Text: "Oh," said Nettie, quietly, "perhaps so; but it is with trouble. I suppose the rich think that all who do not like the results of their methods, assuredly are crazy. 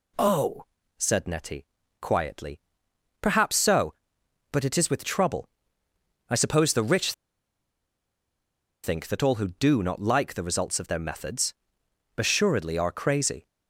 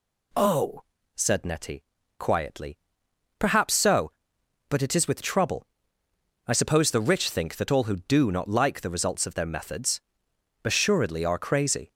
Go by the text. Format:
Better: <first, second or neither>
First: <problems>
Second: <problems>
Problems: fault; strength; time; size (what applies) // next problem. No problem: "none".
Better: second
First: pauses between "rich" and "think"; strong; at 7.1 s; 1.7 s long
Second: none